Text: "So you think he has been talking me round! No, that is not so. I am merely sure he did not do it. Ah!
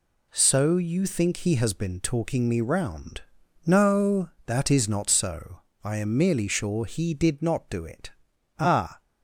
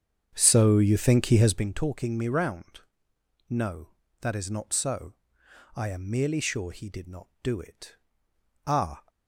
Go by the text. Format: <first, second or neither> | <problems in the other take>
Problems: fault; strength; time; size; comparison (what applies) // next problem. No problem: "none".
first | starts louder than the rest; strong; until 1.8 s; 8 dB